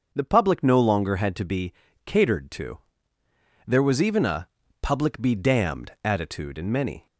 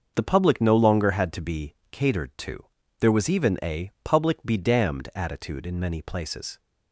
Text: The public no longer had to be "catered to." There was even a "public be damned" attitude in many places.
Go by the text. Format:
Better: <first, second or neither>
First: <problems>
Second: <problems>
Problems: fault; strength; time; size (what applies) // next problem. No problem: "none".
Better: second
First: starts louder than the rest; until 1.1 s; 6.5 dB // pauses between "be" and "catered"; slight; at 1.7 s; 0.32 s long // pauses between "a" and "public"; slight; at 4.4 s; 0.36 s long // stops before "places"; at 7.0 s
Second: starts louder than the rest; until 1.1 s; 6 dB // pauses between "be" and "catered"; slight; at 1.7 s; 0.16 s long